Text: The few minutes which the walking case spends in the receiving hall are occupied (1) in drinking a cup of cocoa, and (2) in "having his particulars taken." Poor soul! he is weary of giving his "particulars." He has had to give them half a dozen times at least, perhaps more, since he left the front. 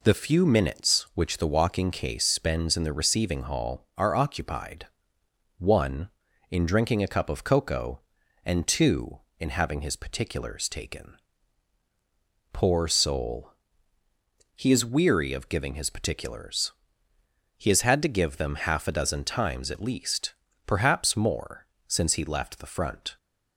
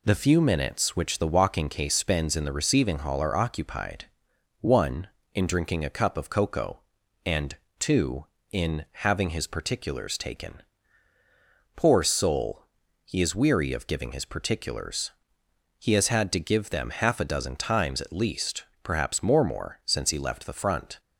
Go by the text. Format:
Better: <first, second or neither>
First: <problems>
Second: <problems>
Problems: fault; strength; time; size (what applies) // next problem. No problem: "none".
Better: first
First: none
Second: says "more" twice; at 19.4 s